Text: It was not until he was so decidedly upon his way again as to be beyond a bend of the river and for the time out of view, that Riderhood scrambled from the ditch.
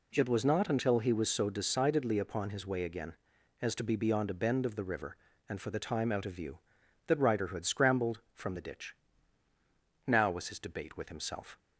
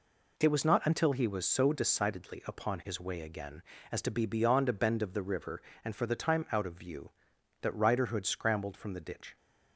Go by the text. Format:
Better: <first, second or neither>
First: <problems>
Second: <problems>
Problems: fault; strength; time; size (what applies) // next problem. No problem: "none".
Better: second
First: goes on to say "Now was his debate with himself"; from 10.0 s on; 1.5 s long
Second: none